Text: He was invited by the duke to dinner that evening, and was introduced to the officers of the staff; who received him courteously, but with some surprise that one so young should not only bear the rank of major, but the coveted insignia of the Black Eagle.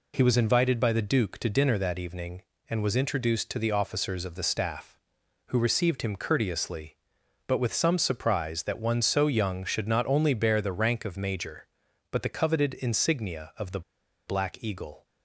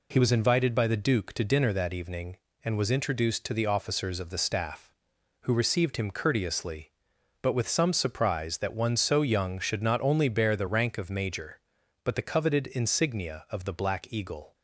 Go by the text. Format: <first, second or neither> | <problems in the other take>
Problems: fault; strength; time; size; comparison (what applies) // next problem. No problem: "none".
second | pauses between "the" and "Black"; noticeable; at 13.8 s; 0.46 s long